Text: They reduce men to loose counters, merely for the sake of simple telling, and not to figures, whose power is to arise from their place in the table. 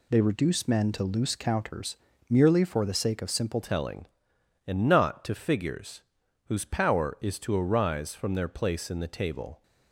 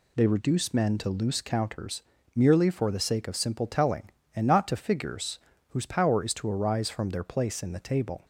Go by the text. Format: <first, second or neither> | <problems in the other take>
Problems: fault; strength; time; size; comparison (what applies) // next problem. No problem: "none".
second | changes voice at "telling"; from 3.6 s on; 6.0 s long